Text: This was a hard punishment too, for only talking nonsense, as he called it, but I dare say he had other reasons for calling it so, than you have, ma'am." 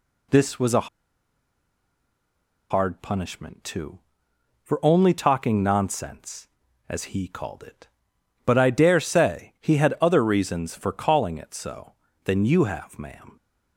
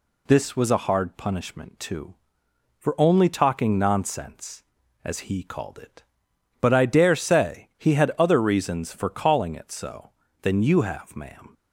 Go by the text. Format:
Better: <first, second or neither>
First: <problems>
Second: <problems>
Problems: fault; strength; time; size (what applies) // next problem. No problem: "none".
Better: second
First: pauses between "a" and "hard"; strong; at 0.8 s; 1.8 s long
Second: none